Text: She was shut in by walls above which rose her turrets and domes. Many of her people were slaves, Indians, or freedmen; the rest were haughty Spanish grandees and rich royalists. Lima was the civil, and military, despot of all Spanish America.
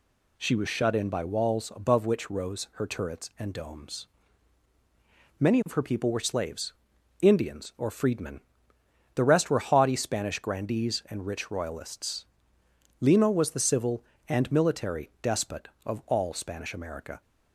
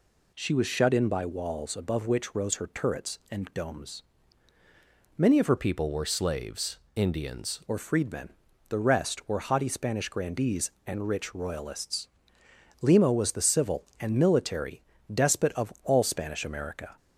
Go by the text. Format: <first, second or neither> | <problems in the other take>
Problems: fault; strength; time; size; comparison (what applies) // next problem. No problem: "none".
first | changes voice from "people" to "Indians"; from 5.5 to 7.6 s; 2.1 s long